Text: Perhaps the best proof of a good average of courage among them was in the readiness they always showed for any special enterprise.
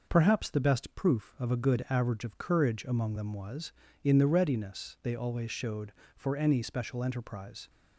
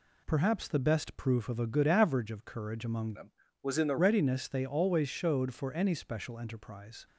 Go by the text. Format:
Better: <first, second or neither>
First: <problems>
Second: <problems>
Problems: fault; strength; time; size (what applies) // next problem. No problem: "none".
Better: first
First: none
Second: changes voice from "them" to "the"; from 3.1 to 3.9 s; 0.8 s long